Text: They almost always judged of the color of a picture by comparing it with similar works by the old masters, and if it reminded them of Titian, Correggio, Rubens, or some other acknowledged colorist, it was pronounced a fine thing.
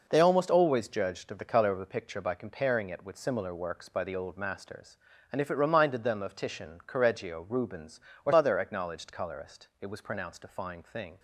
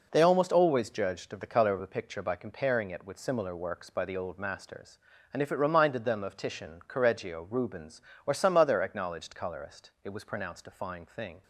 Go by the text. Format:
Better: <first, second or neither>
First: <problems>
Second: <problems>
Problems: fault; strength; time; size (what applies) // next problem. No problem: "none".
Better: second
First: skips "some"; at 8.3 s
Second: none